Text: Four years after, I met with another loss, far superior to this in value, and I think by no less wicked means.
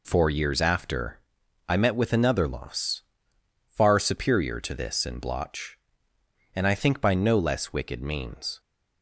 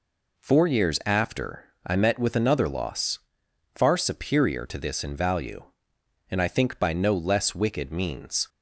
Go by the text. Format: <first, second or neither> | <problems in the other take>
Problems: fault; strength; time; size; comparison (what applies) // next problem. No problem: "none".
second | says "blotch" for "value"; at 5.1 s